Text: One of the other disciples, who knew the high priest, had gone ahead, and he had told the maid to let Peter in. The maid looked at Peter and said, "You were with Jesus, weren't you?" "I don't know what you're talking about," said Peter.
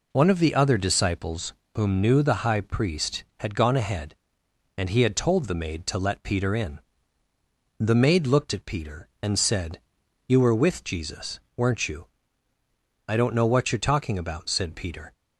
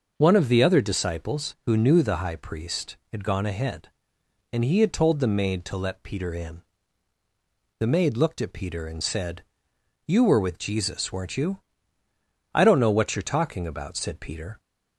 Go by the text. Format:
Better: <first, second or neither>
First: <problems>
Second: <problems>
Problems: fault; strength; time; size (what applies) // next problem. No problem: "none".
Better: second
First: says "whom" for "who"; at 1.7 s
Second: none